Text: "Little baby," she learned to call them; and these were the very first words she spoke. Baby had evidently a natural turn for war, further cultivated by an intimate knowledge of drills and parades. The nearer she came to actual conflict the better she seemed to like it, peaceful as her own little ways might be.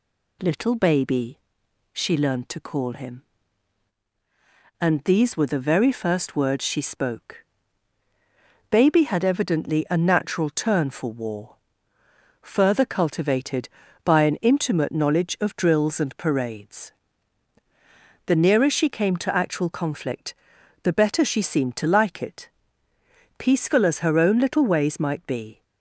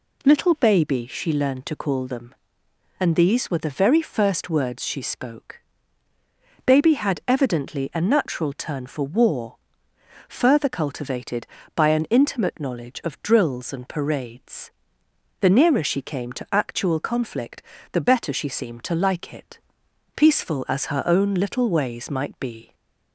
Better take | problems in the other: second | says "him" for "them"; at 2.9 s // pauses between "conflict" and "the"; noticeable; at 20.3 s; 0.48 s long; slight in the second

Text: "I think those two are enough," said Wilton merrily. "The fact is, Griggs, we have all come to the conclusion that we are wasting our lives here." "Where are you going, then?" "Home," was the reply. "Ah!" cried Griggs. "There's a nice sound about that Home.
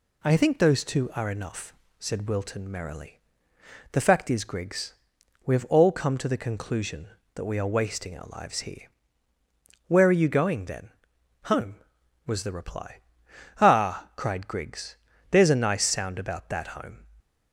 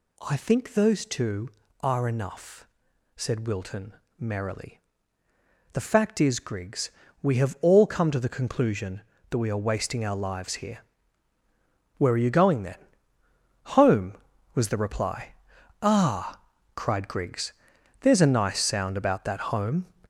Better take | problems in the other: first | gets louder; noticeable; throughout; 5.5 dB // pauses between "Wilton" and "merrily"; slight; at 3.9 s; 0.24 s long

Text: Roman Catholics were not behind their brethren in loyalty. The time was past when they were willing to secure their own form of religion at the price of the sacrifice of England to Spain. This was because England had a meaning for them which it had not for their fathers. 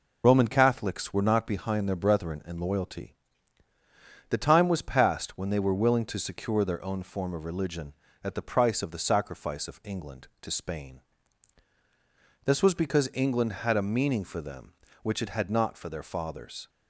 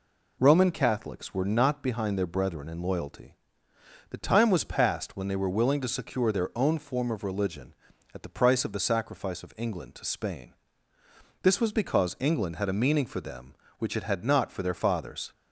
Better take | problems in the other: second | loses the start of "Roman"; at 0.2 s; 30 ms

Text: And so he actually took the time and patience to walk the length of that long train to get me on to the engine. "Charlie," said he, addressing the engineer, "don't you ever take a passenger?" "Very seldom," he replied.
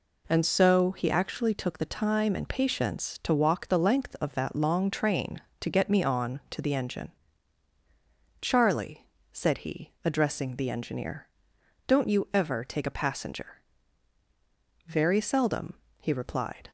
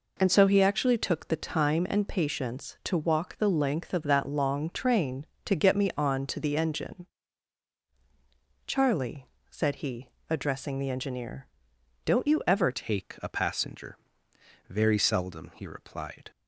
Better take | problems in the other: first | changes voice at "take"; from 12.7 s on; 3.6 s long

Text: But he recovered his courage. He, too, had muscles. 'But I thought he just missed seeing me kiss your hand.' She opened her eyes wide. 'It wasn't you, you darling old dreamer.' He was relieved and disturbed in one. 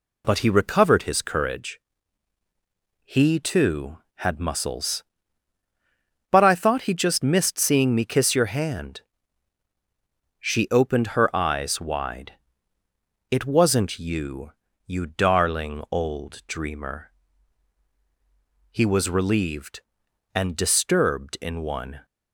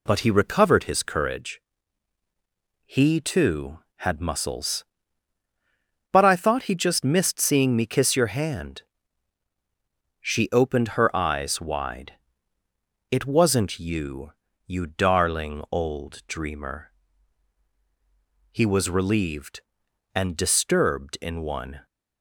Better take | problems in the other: neither | none

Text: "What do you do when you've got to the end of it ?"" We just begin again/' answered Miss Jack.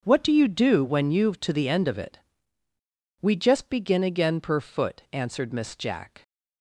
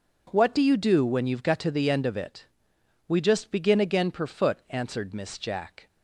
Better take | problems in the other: second | starts louder than the rest; until 1.0 s; 6 dB // skips "got"; at 1.3 s

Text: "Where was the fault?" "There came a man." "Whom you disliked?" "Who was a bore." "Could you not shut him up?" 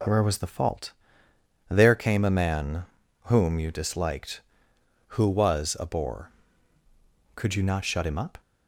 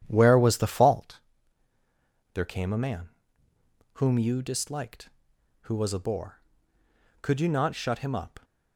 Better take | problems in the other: first | starts louder than the rest; strong; until 1.2 s; 10 dB

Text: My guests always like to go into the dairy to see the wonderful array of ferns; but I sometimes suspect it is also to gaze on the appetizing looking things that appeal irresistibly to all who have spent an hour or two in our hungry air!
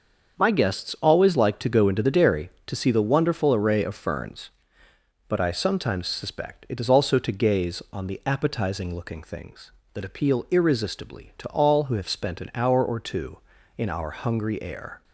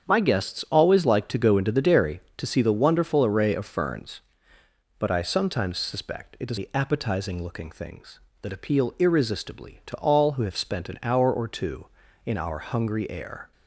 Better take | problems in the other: first | starts louder than the rest; strong; until 1.0 s; 7.5 dB; also in the first // skips "also to gaze on"; at 6.5 s

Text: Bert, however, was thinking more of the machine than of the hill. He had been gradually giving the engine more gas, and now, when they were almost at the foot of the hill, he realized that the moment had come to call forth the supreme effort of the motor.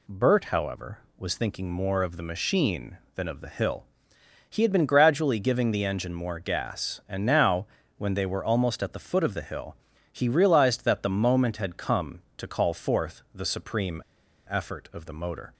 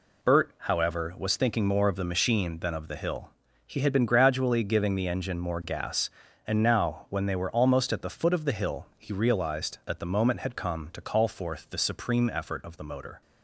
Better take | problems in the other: second | pauses between "supreme" and "effort"; noticeable; at 14.0 s; 0.46 s long

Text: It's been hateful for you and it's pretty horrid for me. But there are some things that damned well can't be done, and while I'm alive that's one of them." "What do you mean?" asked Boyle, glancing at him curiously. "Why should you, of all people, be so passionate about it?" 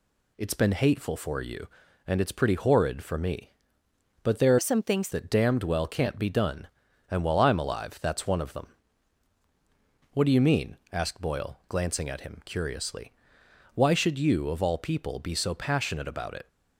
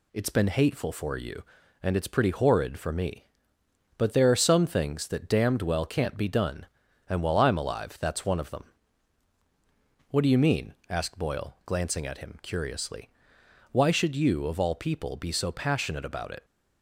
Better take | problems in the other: second | changes voice from "are" to "things"; from 4.5 to 5.0 s; 0.5 s long

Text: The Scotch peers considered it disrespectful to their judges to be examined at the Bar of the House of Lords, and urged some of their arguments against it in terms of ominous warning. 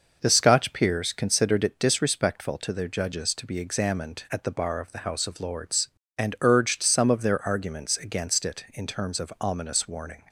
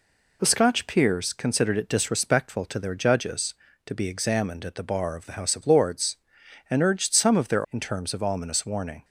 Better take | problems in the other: first | skips "arguments against it"; at 7.6 s

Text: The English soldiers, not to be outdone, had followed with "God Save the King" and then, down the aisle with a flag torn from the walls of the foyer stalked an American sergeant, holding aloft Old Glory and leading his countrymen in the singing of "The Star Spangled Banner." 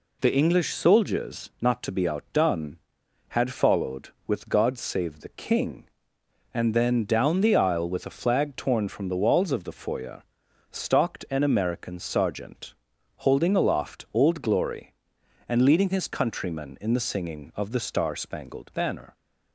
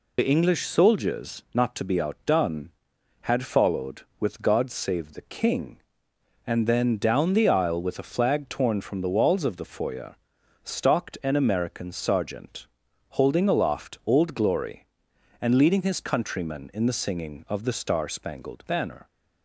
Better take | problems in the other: first | loses the start of "The"; at 0.1 s; 45 ms // pauses between "foyer" and "stalked"; noticeable; at 10.1 s; 0.48 s long; noticeable in the first

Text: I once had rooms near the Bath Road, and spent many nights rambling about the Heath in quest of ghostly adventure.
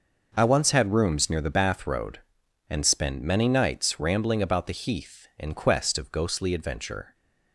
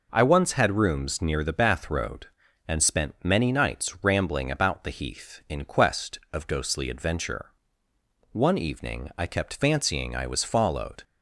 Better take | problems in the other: first | goes on to say "One evening I kept fancying I was followed"; strong; from 8.3 s on; 2.7 s long

